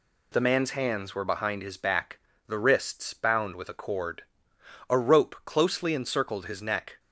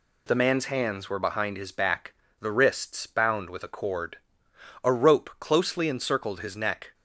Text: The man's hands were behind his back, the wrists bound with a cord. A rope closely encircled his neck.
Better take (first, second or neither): neither